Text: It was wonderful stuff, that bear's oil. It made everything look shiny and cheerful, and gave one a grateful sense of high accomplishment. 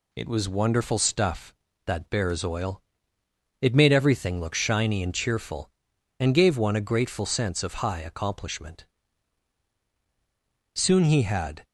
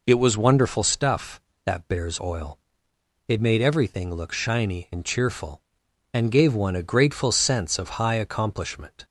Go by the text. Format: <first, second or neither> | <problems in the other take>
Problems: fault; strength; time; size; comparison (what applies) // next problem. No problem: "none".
second | goes on to say "Soon he had"; noticeable; from 10.7 s on; 0.90 s long